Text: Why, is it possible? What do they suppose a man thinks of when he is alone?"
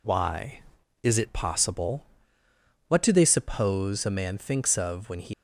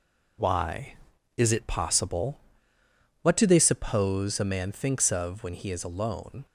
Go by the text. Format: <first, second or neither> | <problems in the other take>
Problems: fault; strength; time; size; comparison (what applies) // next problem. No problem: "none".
second | stops before "is alone"; at 5.3 s